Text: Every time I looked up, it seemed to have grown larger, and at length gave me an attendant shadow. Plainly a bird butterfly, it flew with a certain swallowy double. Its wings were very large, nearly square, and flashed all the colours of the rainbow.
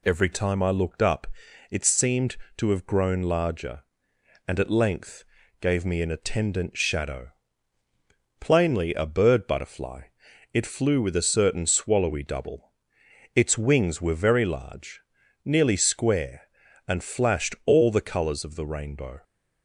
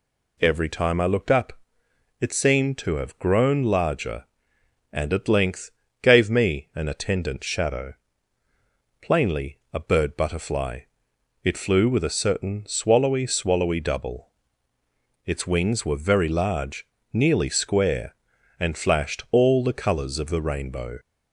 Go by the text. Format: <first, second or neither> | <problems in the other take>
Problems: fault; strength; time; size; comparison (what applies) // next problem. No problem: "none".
first | pauses between "length" and "gave"; slight; at 5.7 s; 0.30 s long; also in the first // pauses between "Plainly" and "a"; slight; at 9.5 s; 0.16 s long // says "swallowy" twice; at 13.2 s